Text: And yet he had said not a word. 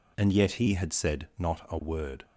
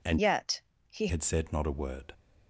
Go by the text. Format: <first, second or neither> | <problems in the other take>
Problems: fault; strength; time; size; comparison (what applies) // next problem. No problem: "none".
first | changes voice from "yet" to "he"; from 0.1 to 1.0 s; 0.9 s long // pauses between "yet" and "he"; slight; at 0.5 s; 0.28 s long